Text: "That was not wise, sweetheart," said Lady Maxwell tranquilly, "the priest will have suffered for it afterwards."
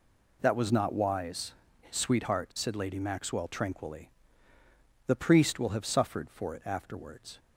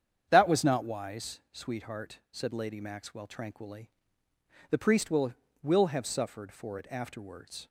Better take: first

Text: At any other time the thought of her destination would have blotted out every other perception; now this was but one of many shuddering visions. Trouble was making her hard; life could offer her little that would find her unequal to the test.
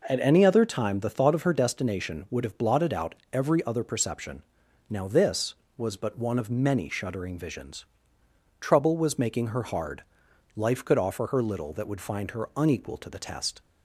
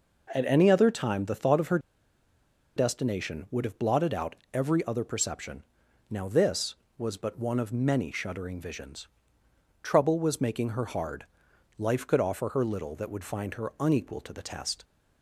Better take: first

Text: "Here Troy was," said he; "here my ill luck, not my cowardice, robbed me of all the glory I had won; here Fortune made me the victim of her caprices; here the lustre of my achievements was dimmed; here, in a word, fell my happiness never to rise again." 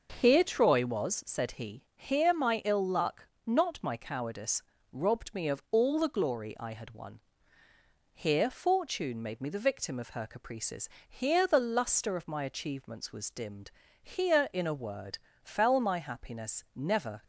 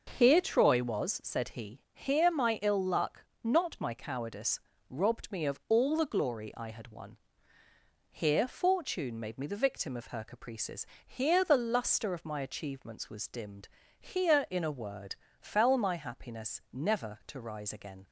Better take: second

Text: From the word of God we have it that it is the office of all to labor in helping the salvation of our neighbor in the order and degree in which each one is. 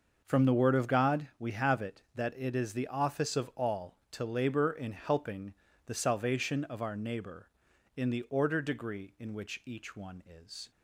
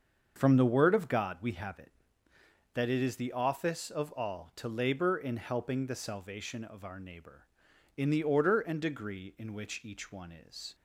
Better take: second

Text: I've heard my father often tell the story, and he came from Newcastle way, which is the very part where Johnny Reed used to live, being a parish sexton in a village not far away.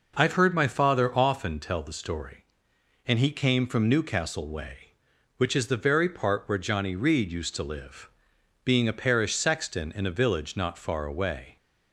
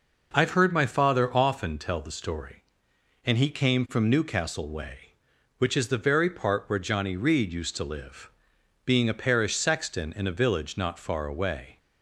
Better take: neither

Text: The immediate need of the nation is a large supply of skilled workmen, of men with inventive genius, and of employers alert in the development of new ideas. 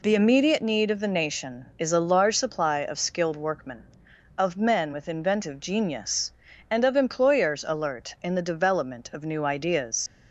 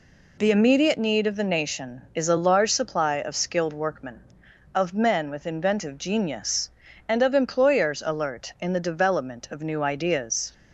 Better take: second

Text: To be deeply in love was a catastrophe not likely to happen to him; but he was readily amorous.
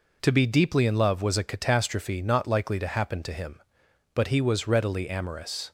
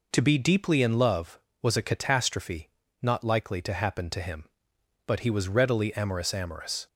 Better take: first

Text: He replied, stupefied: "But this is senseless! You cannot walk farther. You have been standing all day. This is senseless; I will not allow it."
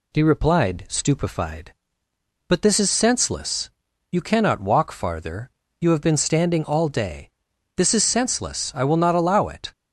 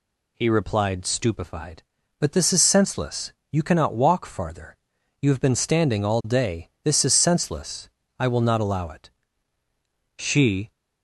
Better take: first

